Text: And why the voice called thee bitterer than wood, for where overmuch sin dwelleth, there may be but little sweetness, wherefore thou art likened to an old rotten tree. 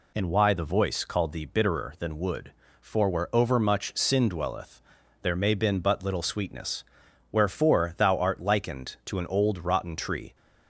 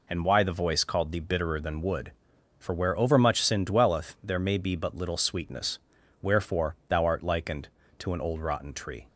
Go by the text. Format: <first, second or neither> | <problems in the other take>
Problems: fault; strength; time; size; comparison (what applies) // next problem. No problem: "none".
second | says "been" for "be"; at 5.5 s